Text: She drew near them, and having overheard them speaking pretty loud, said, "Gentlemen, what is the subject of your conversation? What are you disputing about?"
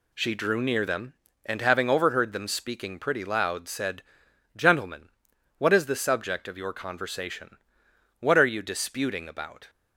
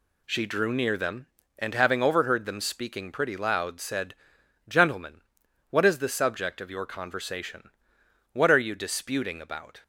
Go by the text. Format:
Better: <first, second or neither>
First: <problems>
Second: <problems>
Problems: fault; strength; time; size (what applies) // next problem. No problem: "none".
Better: neither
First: none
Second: none